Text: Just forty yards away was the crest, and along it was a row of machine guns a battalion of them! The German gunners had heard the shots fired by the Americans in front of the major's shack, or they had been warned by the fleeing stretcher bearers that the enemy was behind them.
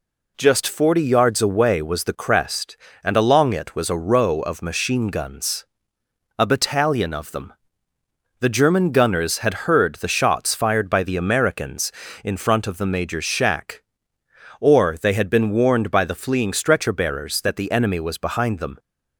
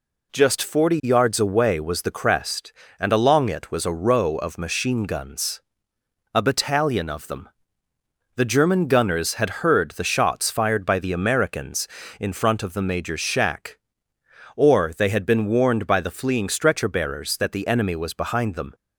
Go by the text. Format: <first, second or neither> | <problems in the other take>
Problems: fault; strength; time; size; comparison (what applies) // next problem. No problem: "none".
neither | pauses between "guns" and "a"; noticeable; the same in both